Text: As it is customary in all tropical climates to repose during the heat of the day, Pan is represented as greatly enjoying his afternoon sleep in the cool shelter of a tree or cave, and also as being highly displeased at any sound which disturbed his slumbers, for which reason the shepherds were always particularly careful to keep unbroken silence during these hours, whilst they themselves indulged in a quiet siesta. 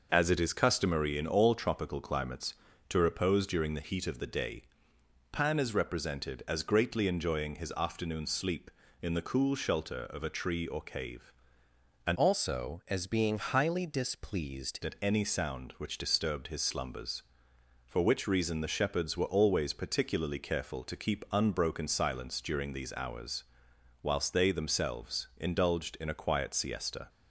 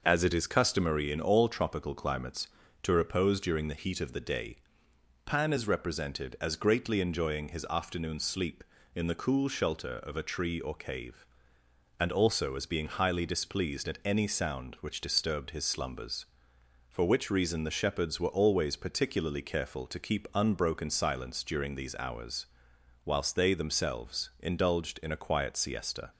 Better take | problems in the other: second | changes voice from "also" to "displeased"; from 12.1 to 14.7 s; 2.6 s long

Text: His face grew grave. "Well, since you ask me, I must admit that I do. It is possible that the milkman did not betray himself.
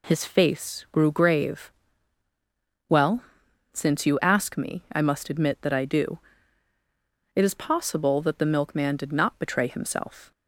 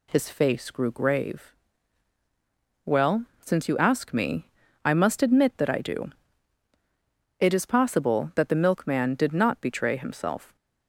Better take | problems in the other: neither | none

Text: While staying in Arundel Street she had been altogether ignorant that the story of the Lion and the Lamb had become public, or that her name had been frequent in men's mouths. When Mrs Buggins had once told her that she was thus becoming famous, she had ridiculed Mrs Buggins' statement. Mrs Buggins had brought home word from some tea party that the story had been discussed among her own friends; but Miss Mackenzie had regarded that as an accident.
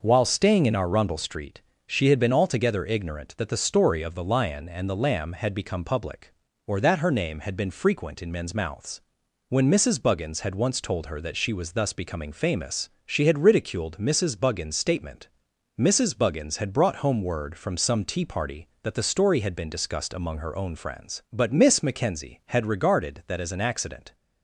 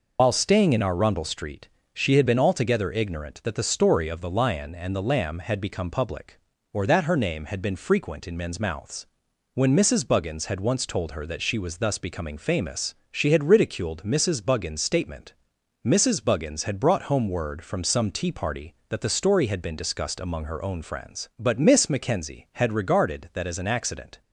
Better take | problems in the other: first | loses the start of "While"; at 0.1 s; 115 ms // pauses between "Street" and "she"; slight; at 1.6 s; 0.24 s long; slight in the first

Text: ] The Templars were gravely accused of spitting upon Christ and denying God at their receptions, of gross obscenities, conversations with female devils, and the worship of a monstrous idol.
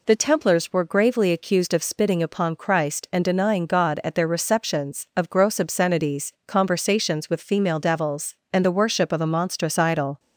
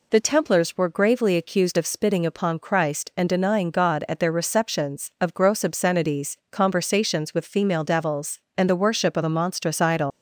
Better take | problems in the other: first | leaves "idol" unfinished; at 10.1 s; 115 ms

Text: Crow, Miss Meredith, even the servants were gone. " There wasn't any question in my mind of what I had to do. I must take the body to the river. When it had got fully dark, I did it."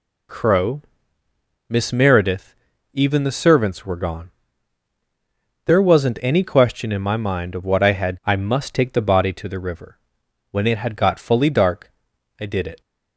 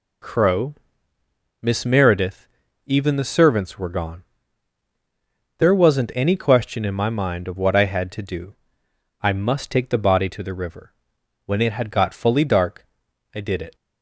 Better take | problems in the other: second | skips "to do"; at 8.2 s

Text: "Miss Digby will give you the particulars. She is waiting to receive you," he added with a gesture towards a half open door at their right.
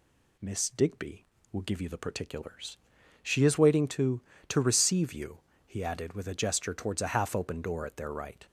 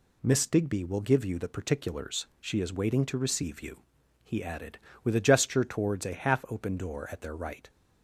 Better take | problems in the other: second | says "to" twice; at 4.4 s

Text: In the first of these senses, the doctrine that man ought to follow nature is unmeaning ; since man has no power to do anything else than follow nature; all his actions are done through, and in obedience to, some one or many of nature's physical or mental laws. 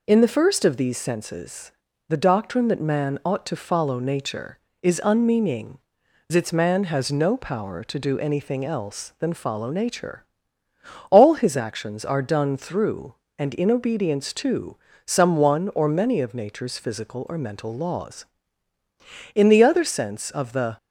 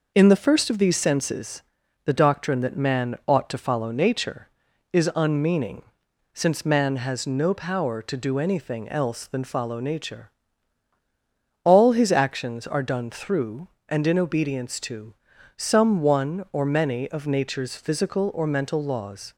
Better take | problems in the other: second | goes on to say "In the other sense of the"; from 19.3 s on; 1.4 s long

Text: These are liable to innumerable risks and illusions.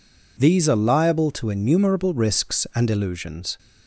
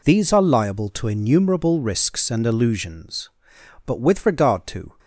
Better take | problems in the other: first | goes on to say "But with regard to"; noticeable; from 3.8 s on; 1.1 s long

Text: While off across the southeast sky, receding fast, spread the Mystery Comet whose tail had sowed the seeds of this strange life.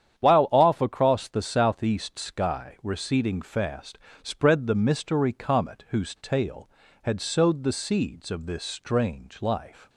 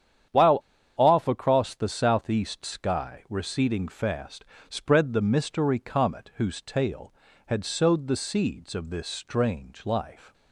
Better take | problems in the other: first | starts louder than the rest; strong; until 1.6 s; 9.5 dB; strong in the first // pauses between "While" and "off"; at 0.6 s; 0.36 s long

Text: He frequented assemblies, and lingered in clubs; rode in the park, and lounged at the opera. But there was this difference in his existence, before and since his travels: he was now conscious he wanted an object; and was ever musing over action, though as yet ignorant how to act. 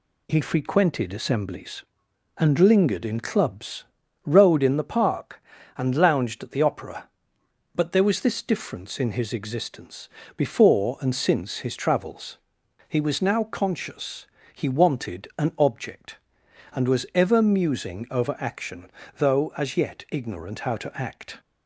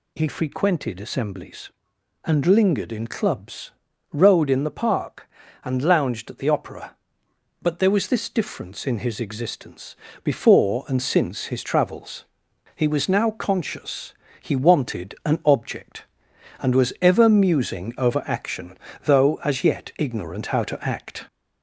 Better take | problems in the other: first | gets louder; slight; throughout; 2.5 dB // pauses between "conscious" and "he"; slight; at 14.1 s; 0.26 s long; slight in the first

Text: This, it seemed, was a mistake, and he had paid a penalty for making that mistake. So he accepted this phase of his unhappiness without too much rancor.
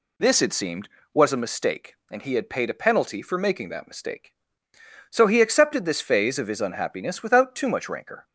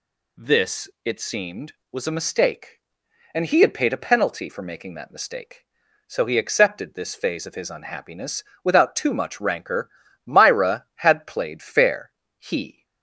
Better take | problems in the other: first | pauses between "unhappiness" and "without"; slight; at 8.4 s; 0.18 s long // goes on to say "Myra had played fair he"; strong; from 10.2 s on; 2.6 s long

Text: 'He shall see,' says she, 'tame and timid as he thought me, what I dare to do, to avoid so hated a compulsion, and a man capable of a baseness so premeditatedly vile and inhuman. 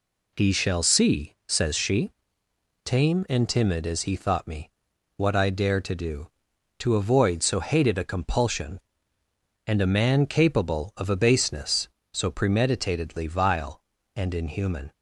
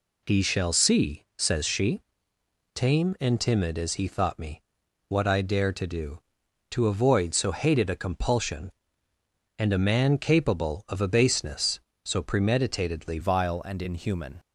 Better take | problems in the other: first | changes voice at "vile"; from 13.2 s on; 1.1 s long

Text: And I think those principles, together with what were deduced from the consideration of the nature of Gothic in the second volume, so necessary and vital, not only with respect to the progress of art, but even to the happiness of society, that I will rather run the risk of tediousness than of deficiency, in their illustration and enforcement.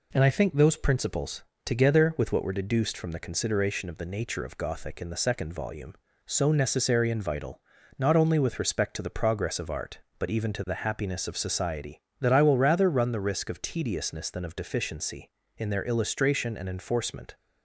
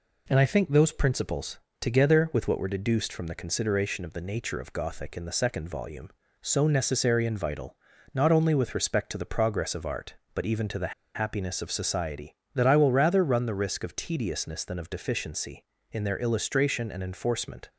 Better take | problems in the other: first | pauses between "the" and "happiness"; slight; at 10.9 s; 0.23 s long

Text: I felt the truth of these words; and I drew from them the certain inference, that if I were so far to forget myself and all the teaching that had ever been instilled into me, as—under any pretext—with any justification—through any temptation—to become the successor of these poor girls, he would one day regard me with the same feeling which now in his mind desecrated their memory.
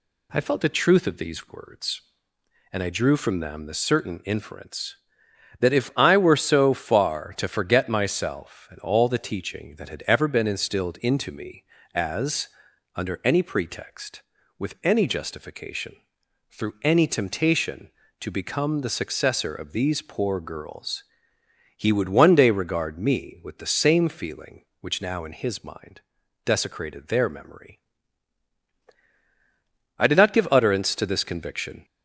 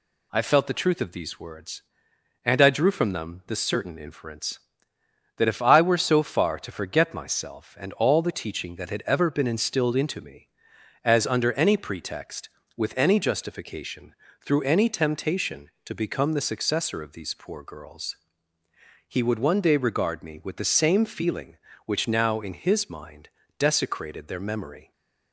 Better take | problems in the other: second | pauses between "mind" and "desecrated"; at 26.0 s; 0.44 s long; slight in the second // goes on to say "I did not give utterance to this conviction"; strong; from 29.9 s on; 1.8 s long

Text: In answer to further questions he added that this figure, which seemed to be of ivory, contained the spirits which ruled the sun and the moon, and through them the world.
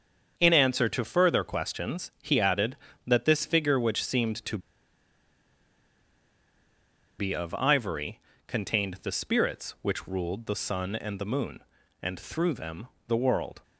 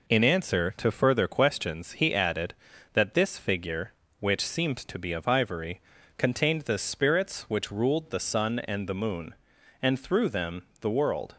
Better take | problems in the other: second | starts louder than the rest; strong; until 1.3 s; 7.5 dB // pauses between "to" and "be"; strong; at 4.5 s; 2.6 s long // pauses between "them" and "the"; slight; at 12.8 s; 0.22 s long; slight in the second

